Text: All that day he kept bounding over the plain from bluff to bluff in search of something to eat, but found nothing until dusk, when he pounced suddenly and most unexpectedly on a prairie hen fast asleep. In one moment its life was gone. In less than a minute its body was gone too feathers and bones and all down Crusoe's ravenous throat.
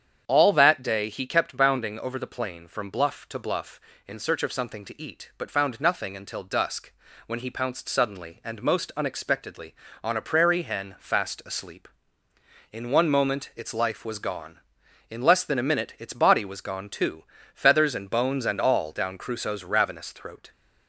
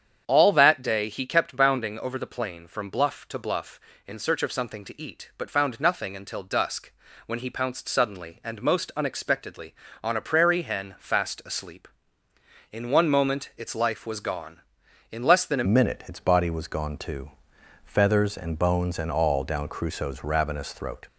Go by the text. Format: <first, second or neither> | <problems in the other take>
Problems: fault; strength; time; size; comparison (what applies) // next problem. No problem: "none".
first | starts louder than the rest; strong; until 1.2 s; 8 dB; strong in the first // changes voice at "minute"; from 15.6 s on; 5.4 s long // pauses between "too" and "feathers"; noticeable; at 17.2 s; 0.56 s long; slight in the first